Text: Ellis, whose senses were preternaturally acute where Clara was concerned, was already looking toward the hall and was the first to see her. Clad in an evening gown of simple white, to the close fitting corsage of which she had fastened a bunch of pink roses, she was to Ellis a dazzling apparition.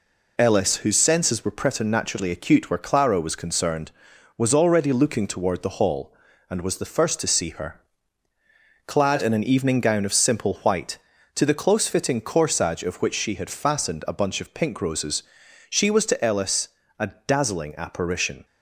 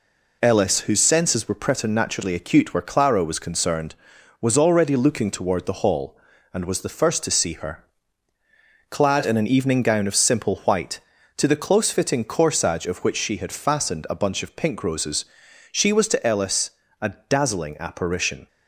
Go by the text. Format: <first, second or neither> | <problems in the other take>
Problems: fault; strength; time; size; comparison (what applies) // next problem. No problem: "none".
neither | pauses between "Ellis" and "a"; slight; the same in both // pauses between "a" and "dazzling"; slight; the same in both